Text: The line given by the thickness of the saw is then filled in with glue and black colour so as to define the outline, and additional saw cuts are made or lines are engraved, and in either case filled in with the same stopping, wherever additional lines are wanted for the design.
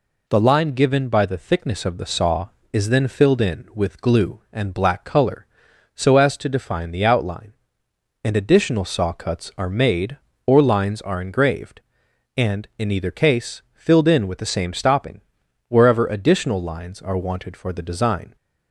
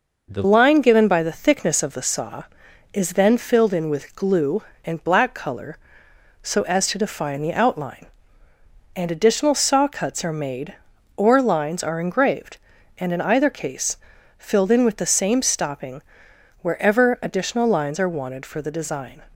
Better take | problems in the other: first | changes voice at "line"; from 0.4 s on; 18.8 s long // pauses between "case" and "filled"; at 13.9 s; 0.42 s long

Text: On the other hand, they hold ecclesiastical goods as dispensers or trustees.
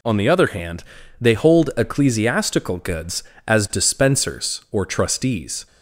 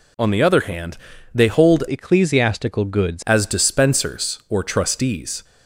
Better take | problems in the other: first | changes voice from "ecclesiastical" to "goods"; from 1.8 to 3.2 s; 1.4 s long

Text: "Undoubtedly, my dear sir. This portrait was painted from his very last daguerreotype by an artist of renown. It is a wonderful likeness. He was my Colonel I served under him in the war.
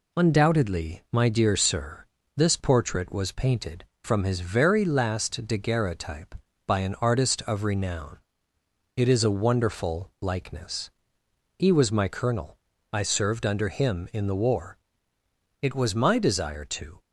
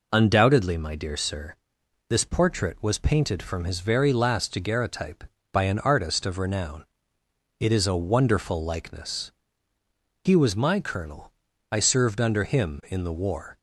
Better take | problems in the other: second | pauses between "Colonel" and "I"; slight; at 12.5 s; 0.34 s long; also in the second // goes on to say "It was my desire to"; from 15.6 s on; 1.4 s long

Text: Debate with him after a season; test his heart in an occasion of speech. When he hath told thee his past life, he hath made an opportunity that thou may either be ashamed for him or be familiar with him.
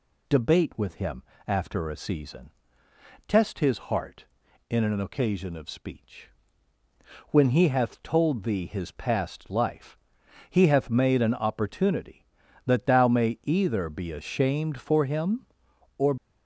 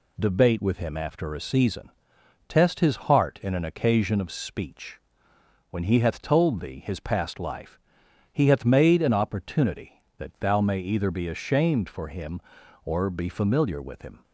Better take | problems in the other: second | pauses between "him" and "after"; slight; at 1.2 s; 0.24 s long // stops before "be familiar with him"; at 16.1 s

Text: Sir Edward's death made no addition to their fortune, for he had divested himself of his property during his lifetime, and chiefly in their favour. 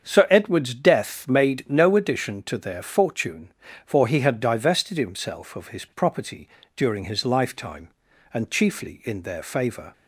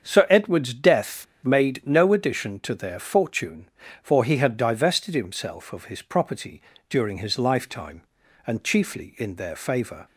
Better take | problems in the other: first | starts louder than the rest; strong; until 1.0 s; 7 dB; strong in the first // pauses between "death" and "made"; slight; at 1.2 s; 0.17 s long // pauses between "property" and "during"; slight; at 6.6 s; 0.28 s long; slight in the first

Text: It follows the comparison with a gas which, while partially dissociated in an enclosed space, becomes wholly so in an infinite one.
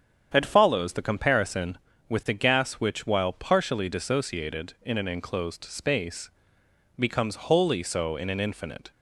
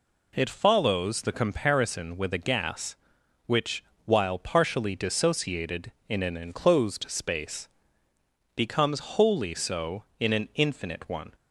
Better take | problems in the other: second | starts louder than the rest; strong; until 1.3 s; 8 dB // stops before "one"; at 8.9 s

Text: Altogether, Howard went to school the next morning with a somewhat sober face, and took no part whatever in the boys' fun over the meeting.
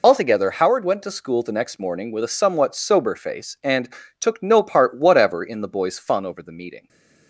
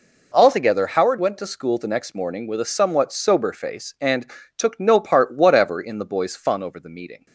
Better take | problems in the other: second | loses the start of "Altogether"; at 0.0 s; 75 ms // pauses between "and" and "took"; slight; at 3.8 s; 0.30 s long; slight in the second // stays silent after the last word; slight; from 6.7 s on; 0.5 s long

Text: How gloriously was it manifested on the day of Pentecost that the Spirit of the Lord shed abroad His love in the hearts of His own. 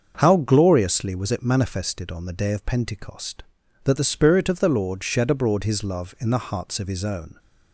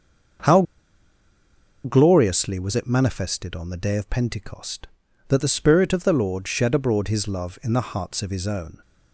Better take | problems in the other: first | starts louder than the rest; until 2.6 s; 6.5 dB; also in the first // pauses between "How" and "gloriously"; at 0.6 s; 1.2 s long

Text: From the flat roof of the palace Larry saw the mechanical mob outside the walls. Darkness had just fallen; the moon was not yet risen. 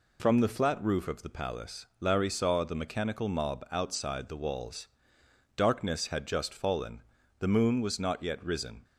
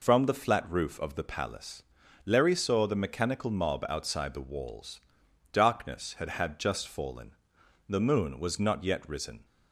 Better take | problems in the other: first | pauses between "palace" and "Larry"; at 1.8 s; 0.42 s long // says "had" twice; at 6.3 s

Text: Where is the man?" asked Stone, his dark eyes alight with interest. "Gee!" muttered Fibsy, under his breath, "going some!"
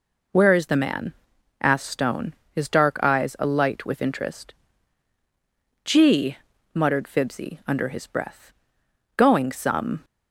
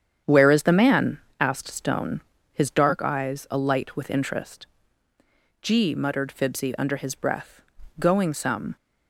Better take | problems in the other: first | starts louder than the rest; strong; until 1.4 s; 8.5 dB

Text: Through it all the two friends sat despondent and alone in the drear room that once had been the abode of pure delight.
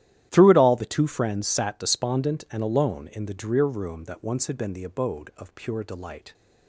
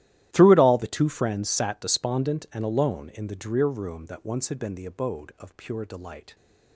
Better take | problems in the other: first | gets quieter; strong; throughout; 19.5 dB // starts louder than the rest; strong; until 1.3 s; 13.5 dB; strong in the first

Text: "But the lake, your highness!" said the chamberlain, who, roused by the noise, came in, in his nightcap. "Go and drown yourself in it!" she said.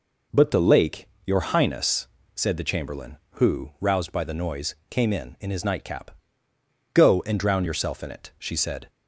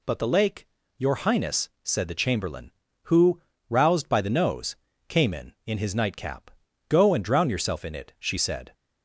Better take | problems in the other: first | says "nose" for "noise"; at 4.3 s

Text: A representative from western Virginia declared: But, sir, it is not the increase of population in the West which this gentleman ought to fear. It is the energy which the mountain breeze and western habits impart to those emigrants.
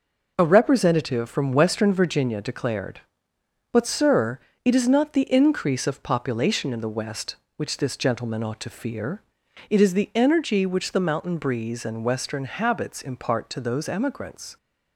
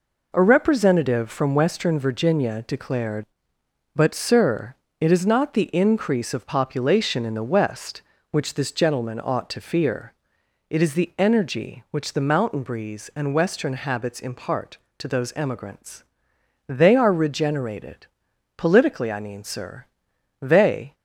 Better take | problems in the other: first | goes on to say "They are regenerated politically I mean sir They"; strong; from 16.6 s on; 4.2 s long

